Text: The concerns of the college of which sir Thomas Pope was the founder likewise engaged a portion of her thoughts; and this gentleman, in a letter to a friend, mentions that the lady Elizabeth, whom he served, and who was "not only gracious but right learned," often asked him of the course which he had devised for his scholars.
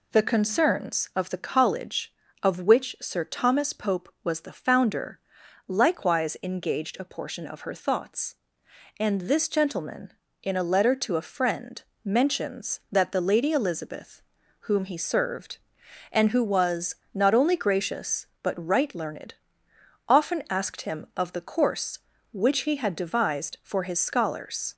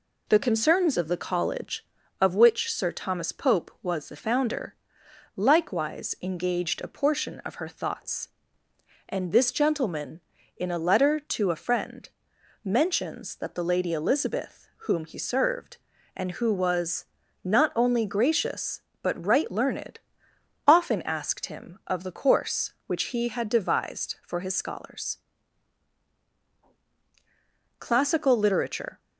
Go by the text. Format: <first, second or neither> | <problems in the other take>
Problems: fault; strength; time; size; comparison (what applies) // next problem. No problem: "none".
first | pauses between "founder" and "likewise"; noticeable; at 4.7 s; 0.62 s long; noticeable in the first // pauses between "was" and "not"; at 17.0 s; 0.40 s long; slight in the first // goes on to say "Classical literature"; noticeable; from 27.7 s on; 1.2 s long